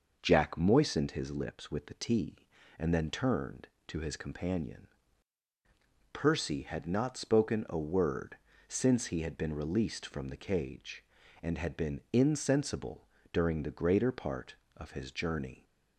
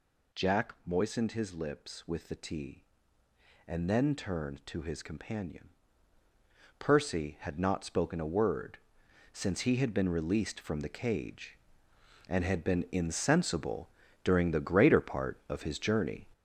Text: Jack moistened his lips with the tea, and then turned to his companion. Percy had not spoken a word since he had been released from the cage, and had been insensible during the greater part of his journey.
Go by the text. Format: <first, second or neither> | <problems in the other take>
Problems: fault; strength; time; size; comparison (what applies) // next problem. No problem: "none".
first | gets louder; throughout; 6.5 dB // pauses between "word" and "since"; noticeable; at 8.7 s; 0.56 s long; slight in the first // pauses between "insensible" and "during"; slight; at 13.8 s; 0.36 s long; slight in the first